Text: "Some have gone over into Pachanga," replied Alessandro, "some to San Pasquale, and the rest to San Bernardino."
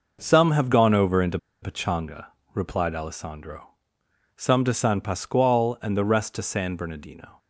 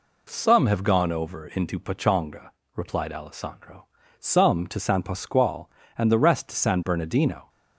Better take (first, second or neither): second